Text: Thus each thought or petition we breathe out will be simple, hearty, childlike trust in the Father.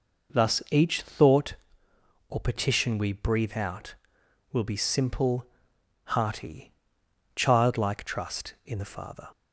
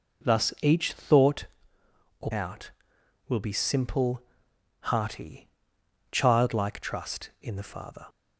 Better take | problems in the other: first | skips "petition we breathe"; at 2.3 s

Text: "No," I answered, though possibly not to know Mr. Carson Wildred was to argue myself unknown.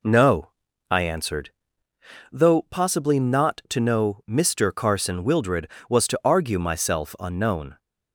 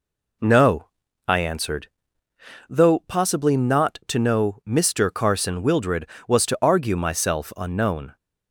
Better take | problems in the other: neither | none

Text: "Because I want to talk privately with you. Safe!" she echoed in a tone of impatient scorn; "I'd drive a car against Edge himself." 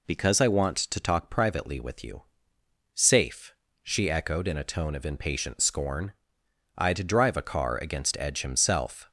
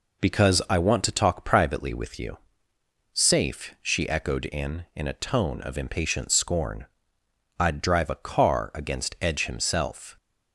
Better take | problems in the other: first | says "in" twice; at 4.9 s

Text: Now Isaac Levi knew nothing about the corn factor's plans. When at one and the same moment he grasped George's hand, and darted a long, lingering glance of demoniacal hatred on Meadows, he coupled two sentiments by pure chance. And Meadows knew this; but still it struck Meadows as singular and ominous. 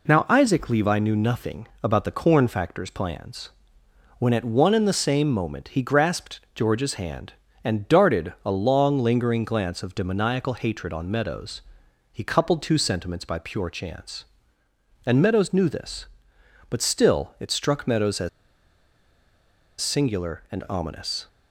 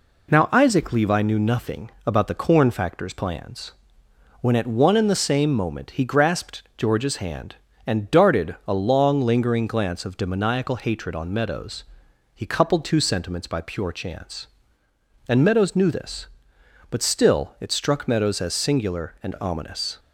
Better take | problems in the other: second | pauses between "nothing" and "about"; slight; at 1.6 s; 0.16 s long; slight in the second // pauses between "grasped" and "George's"; slight; at 6.3 s; 0.16 s long; slight in the second // pauses between "as" and "singular"; strong; at 18.2 s; 1.5 s long

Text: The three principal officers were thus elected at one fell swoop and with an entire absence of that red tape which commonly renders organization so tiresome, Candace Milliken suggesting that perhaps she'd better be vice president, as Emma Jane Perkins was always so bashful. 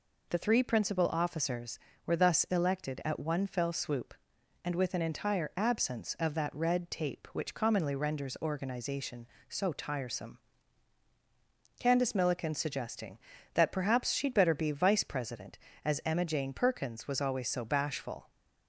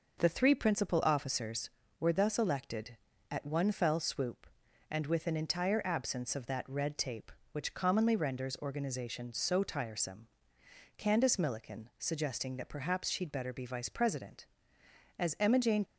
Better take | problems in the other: first | stops before "Perkins was always so bashful"; at 15.8 s

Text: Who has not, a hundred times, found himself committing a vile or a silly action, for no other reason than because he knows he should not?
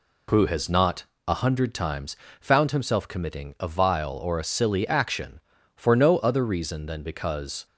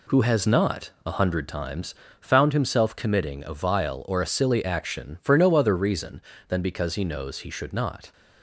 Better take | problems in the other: second | stops before "he knows he should not"; at 7.6 s

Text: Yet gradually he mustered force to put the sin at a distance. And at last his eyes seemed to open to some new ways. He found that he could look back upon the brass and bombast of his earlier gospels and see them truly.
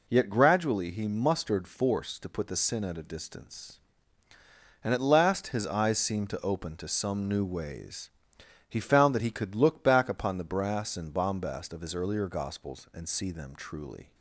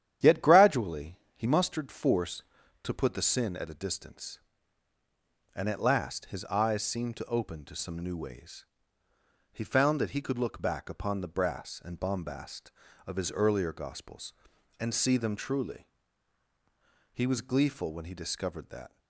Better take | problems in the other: first | starts louder than the rest; strong; until 1.3 s; 10 dB // pauses between "gradually" and "he"; slight; at 1.1 s; 0.16 s long // goes on to say "He was gleeful when he discovered that"; strong; from 17.1 s on; 1.8 s long

